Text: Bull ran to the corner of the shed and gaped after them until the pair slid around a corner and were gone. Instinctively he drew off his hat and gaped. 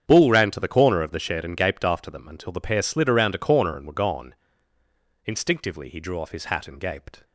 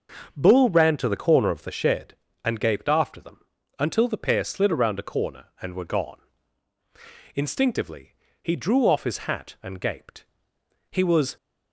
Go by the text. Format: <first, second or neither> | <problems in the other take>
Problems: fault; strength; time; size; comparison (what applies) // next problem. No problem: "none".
first | starts louder than the rest; until 1.3 s; 6.5 dB; strong in the first // pauses between "them" and "until"; at 3.4 s; 0.38 s long // pauses between "Instinctively" and "he"; slight; at 8.1 s; 0.28 s long // goes on to say "He was"; slight; from 10.9 s on; 0.46 s long